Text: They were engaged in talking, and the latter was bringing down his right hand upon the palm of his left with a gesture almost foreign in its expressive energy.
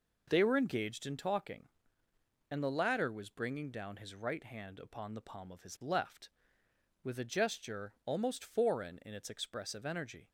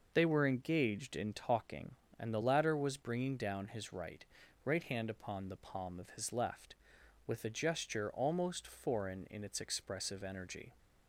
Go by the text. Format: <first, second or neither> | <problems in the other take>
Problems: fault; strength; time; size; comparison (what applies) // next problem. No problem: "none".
first | says "right" twice; at 4.6 s